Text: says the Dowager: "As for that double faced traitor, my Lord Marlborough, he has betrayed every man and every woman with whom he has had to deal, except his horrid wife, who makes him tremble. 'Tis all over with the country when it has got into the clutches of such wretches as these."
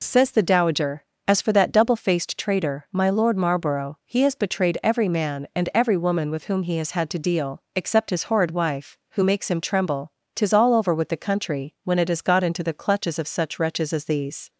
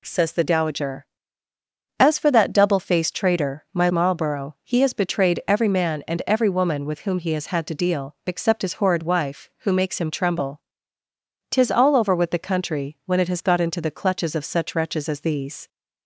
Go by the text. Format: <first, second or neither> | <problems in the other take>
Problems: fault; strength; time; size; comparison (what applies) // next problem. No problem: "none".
first | skips "Lord"; at 3.8 s